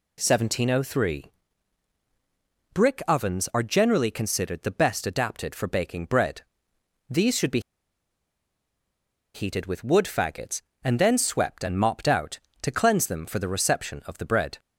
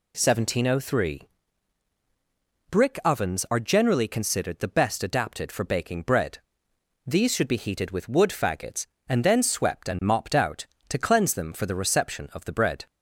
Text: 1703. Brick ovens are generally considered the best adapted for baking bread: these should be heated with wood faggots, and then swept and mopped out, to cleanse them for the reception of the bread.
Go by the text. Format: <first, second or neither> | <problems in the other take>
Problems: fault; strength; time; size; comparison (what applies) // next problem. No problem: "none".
second | pauses between "be" and "heated"; strong; at 7.6 s; 1.7 s long